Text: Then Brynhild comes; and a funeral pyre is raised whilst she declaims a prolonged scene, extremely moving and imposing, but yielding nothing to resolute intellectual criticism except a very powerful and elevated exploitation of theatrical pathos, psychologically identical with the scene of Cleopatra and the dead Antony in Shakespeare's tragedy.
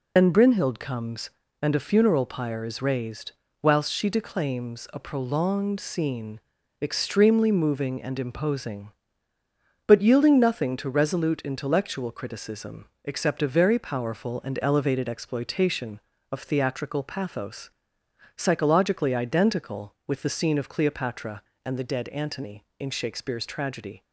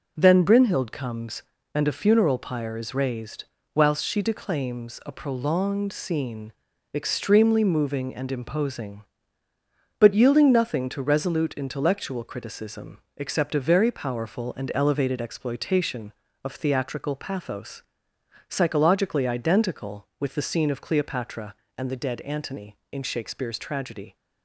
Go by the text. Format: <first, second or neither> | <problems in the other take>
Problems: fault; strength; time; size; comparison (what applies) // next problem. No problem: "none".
second | loses the start of "Then"; at 0.1 s; 105 ms // pauses between "raised" and "whilst"; slight; at 3.3 s; 0.30 s long; slight in the second // pauses between "criticism" and "except"; slight; at 12.8 s; 0.16 s long; slight in the second